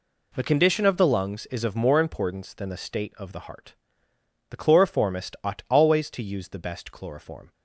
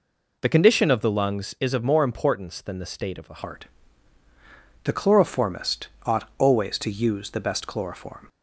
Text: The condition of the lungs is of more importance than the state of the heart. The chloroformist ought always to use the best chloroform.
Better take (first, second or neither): first